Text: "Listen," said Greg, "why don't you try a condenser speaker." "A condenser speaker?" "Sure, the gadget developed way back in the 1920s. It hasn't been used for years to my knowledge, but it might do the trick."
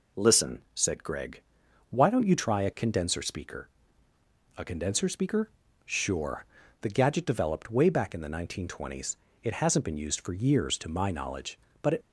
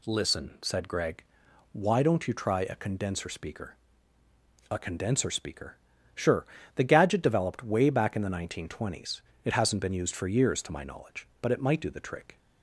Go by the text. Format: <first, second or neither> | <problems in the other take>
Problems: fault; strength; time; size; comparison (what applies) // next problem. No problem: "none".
second | stops before "might do the trick"; at 12.0 s